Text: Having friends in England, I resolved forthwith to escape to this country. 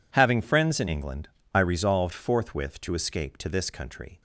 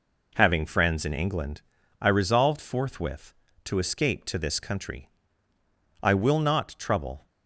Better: first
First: none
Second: goes on to say "I will not trouble"; noticeable; from 6.0 s on; 1.2 s long

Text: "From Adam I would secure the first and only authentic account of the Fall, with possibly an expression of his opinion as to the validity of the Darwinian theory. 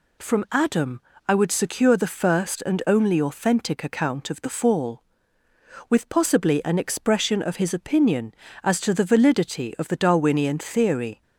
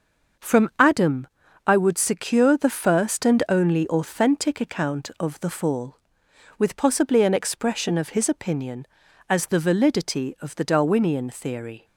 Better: first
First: pauses between "Adam" and "I"; slight; at 1.0 s; 0.26 s long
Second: starts louder than the rest; until 1.8 s; 6 dB // pauses between "Adam" and "I"; at 1.2 s; 0.40 s long // skips "to"; at 9.4 s

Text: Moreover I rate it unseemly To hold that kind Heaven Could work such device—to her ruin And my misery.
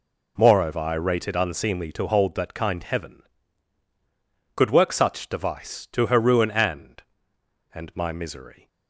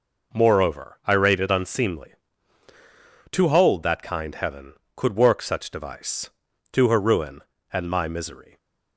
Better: second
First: says "And" twice; at 7.7 s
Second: none

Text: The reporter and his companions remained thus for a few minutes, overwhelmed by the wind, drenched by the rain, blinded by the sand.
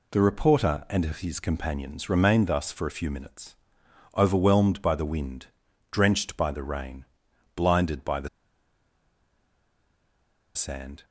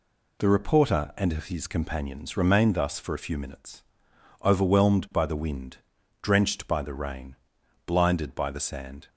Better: second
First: pauses between "the" and "sand"; strong; at 8.2 s; 2.2 s long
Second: none

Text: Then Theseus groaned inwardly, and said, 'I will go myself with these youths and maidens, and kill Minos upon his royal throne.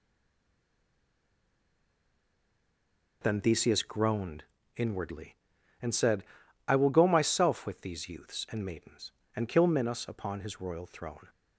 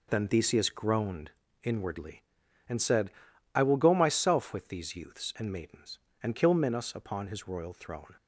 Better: second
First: stays silent before the first word; strong; until 3.2 s; 3.2 s long // pauses between "groaned" and "inwardly"; slight; at 4.4 s; 0.34 s long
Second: pauses between "groaned" and "inwardly"; slight; at 1.2 s; 0.34 s long

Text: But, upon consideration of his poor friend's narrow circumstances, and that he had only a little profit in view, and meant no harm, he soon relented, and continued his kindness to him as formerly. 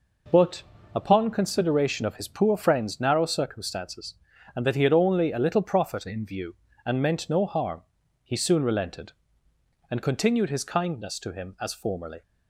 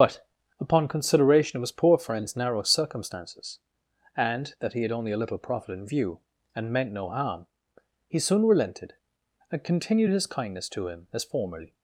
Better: first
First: none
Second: loses the start of "But"; at 0.0 s; 55 ms // starts louder than the rest; until 1.3 s; 6.5 dB

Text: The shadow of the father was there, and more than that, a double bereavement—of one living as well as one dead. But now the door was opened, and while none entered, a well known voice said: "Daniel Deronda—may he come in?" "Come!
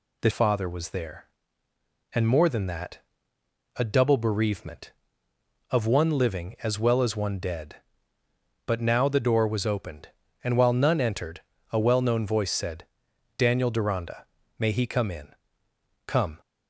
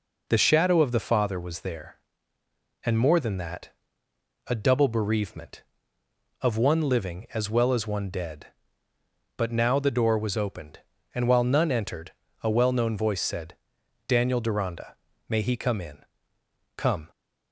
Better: second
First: skips "shadow of the"; at 0.2 s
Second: none

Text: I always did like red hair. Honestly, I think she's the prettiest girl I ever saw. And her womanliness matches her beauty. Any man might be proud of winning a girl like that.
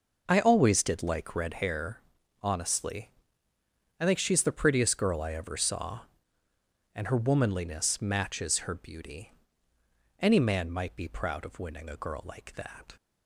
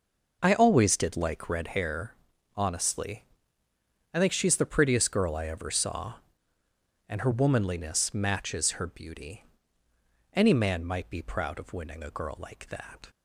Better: neither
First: none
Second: none

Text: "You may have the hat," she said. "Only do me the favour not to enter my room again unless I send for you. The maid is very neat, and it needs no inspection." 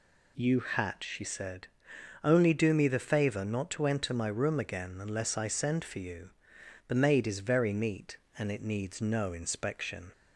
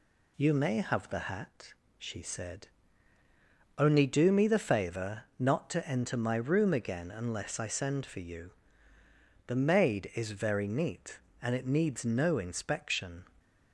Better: second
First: skips "may have the"; at 0.5 s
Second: none

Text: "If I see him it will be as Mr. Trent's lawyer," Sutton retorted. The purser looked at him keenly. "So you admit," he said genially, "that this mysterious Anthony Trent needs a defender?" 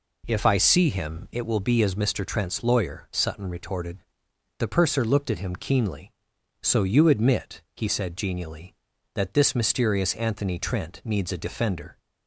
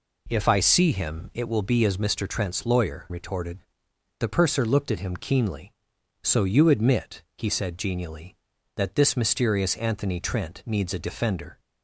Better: first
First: none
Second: skips "Sutton"; at 3.0 s

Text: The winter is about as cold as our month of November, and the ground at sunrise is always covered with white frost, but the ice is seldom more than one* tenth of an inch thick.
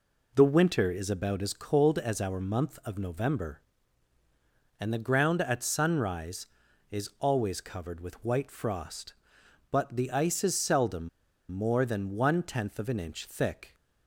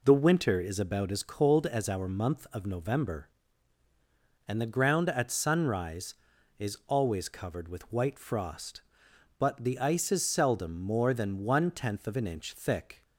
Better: second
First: pauses between "seldom" and "more"; at 11.0 s; 0.41 s long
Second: none

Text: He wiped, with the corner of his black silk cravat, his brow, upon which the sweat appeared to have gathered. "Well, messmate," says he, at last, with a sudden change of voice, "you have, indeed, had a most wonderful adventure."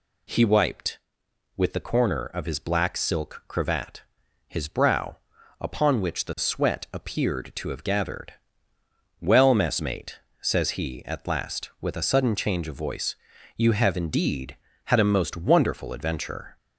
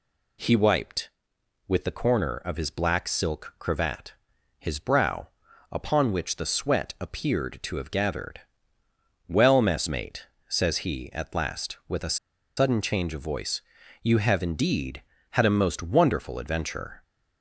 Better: first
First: none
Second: pauses between "a" and "sudden"; at 12.1 s; 0.41 s long

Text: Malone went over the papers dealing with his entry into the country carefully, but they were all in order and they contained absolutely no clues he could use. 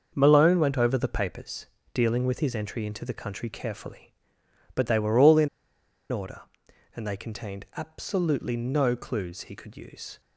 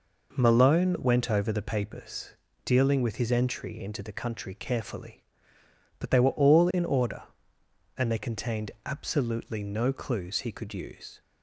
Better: second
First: starts louder than the rest; until 1.1 s; 6.5 dB // pauses between "papers" and "dealing"; slight; at 1.6 s; 0.26 s long // pauses between "in" and "order"; noticeable; at 5.4 s; 0.63 s long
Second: pauses between "papers" and "dealing"; slight; at 2.3 s; 0.28 s long

